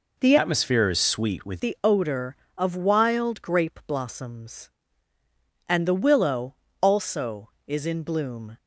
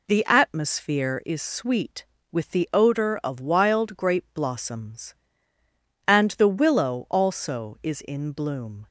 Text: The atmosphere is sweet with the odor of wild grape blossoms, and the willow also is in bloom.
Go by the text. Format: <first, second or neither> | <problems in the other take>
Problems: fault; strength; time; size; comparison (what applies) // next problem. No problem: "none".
second | changes voice from "atmosphere" to "with"; from 0.3 to 1.6 s; 1.3 s long // pauses between "willow" and "also"; slight; at 6.5 s; 0.26 s long